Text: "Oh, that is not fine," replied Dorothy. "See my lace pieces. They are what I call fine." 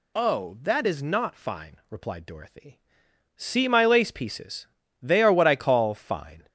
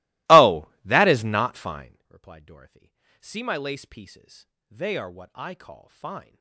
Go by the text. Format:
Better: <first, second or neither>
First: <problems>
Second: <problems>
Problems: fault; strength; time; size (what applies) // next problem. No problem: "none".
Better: first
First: none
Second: starts louder than the rest; strong; until 2.1 s; 20.5 dB